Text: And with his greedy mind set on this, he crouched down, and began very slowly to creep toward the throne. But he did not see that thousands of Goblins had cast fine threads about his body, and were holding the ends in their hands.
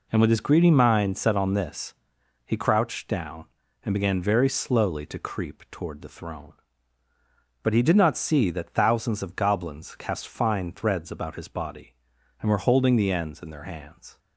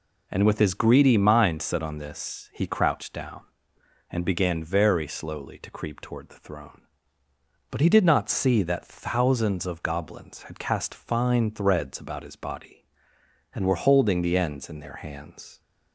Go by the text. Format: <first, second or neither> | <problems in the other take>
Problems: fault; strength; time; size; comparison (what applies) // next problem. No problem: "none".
second | skips "had"; at 9.9 s